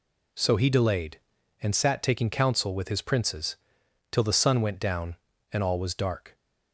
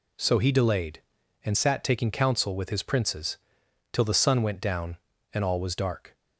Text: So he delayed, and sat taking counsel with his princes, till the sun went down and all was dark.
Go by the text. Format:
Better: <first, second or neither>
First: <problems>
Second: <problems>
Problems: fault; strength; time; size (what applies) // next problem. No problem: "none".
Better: neither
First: none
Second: none